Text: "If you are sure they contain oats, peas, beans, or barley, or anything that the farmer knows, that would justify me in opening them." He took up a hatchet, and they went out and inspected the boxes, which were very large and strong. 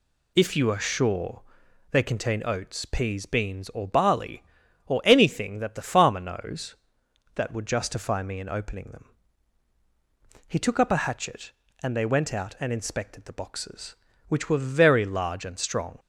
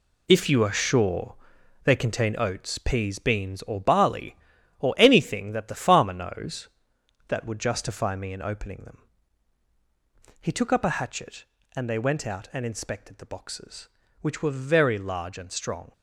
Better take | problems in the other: first | gets quieter; strong; throughout; 9.5 dB // pauses between "sure" and "they"; noticeable; at 1.3 s; 0.48 s long; noticeable in the first

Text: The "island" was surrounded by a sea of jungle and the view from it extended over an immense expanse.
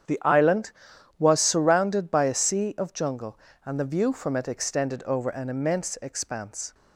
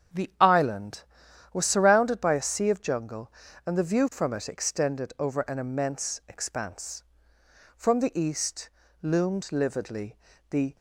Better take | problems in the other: first | starts louder than the rest; strong; until 1.7 s; 8 dB; strong in the first // goes on to say "From the east loomed lividly the"; strong; from 7.7 s on; 3.0 s long

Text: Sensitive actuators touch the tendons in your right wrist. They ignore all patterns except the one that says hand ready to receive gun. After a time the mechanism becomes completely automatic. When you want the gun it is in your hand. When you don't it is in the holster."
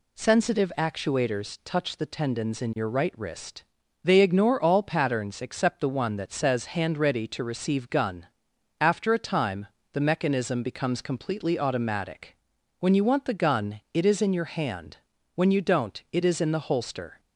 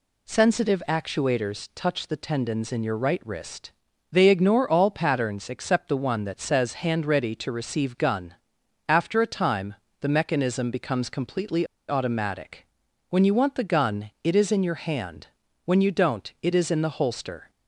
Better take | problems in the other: first | pauses between "time" and "the"; slight; at 9.7 s; 0.24 s long; slight in the first // pauses between "completely" and "automatic"; slight; at 11.6 s; 0.22 s long

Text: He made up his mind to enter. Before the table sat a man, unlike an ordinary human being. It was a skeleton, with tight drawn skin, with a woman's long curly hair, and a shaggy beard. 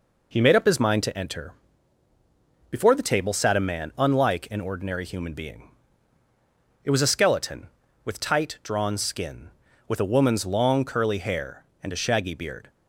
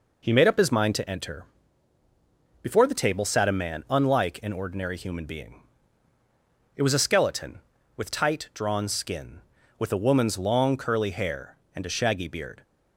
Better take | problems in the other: neither | none

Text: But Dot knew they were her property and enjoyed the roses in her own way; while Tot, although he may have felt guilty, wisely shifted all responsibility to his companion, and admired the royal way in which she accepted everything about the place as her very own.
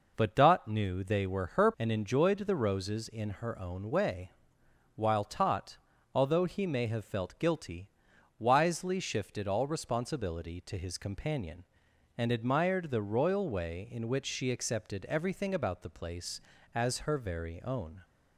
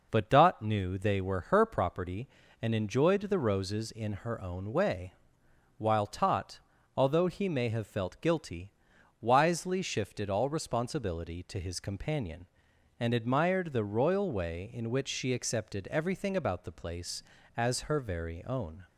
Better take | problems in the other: second | skips "property"; at 1.7 s

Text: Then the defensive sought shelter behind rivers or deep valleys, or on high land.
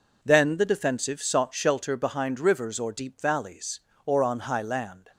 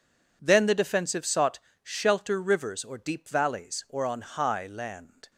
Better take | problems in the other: first | pauses between "sought" and "shelter"; slight; at 1.5 s; 0.24 s long // skips "behind"; at 2.4 s

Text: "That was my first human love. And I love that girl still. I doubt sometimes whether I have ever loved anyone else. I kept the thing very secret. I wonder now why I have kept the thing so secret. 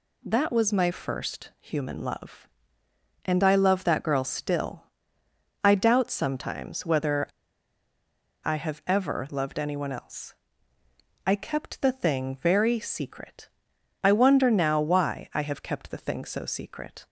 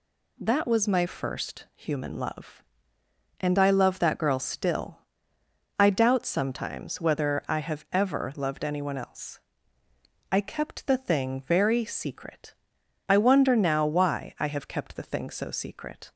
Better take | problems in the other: second | pauses between "whether" and "I"; at 7.2 s; 1.1 s long

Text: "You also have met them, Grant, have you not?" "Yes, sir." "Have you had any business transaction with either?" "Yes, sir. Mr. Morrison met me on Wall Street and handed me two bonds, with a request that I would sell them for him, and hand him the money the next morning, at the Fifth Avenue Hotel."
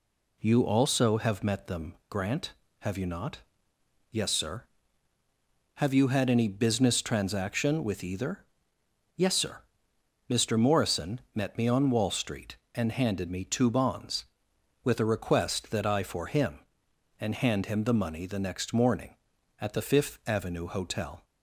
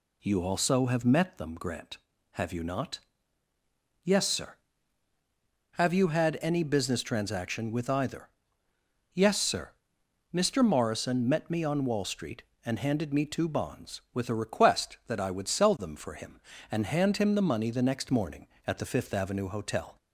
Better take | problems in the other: second | skips "would sell them"; at 16.0 s

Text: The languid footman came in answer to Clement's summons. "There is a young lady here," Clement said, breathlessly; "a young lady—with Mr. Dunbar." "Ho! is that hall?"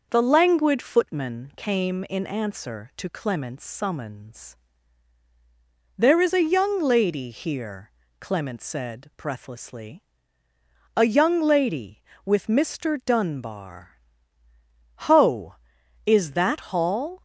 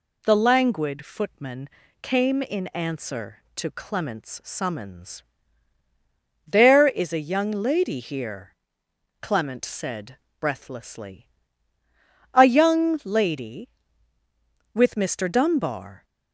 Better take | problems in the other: first | pauses between "footman" and "came"; slight; at 1.6 s; 0.36 s long // stops before "Ho is that hall"; at 16.0 s

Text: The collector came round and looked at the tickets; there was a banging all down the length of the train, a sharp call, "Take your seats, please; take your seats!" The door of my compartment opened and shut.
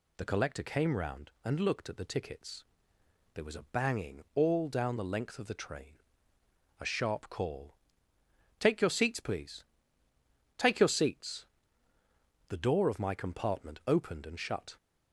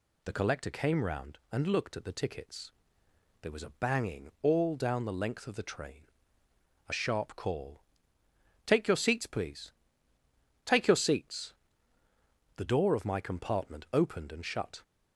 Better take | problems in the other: neither | none

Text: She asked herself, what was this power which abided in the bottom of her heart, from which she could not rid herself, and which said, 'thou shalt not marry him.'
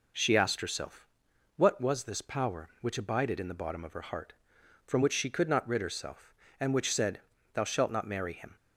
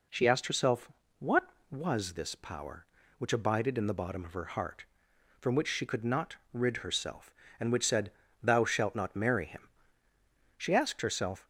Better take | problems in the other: first | pauses between "not" and "rid"; slight; at 6.3 s; 0.16 s long // goes on to say "She asked herself"; noticeable; from 10.5 s on; 0.90 s long

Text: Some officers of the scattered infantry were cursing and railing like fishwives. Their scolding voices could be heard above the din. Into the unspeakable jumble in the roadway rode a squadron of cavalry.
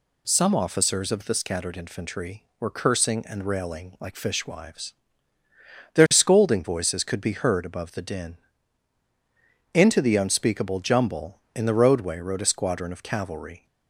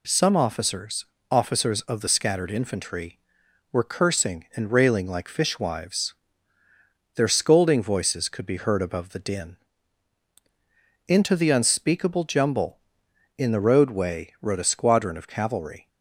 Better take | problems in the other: first | says "officers" twice; at 1.3 s

